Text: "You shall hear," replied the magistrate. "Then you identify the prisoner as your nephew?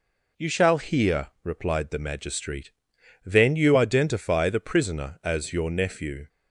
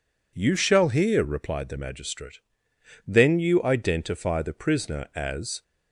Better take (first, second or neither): first